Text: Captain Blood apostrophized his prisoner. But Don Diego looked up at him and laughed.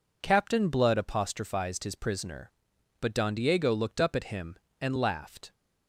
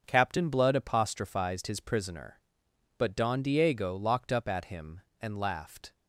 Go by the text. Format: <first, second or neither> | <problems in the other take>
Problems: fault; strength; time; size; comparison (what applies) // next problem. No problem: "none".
first | starts louder than the rest; until 1.0 s; 6.5 dB // says "locked" for "looked"; at 3.9 s